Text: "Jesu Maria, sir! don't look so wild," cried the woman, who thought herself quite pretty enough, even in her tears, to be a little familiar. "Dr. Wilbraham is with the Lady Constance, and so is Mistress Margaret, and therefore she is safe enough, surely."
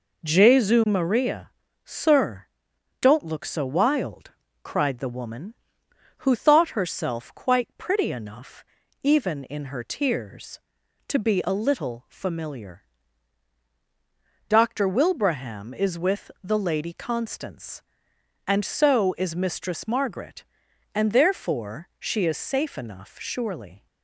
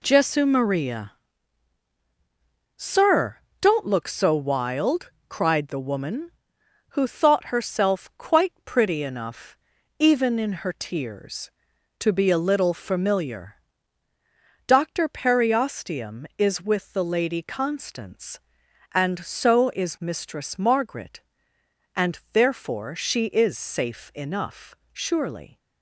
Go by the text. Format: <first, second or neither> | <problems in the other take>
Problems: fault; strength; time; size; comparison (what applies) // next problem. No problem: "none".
first | says "Periosteum" for "Wilbraham"; at 15.0 s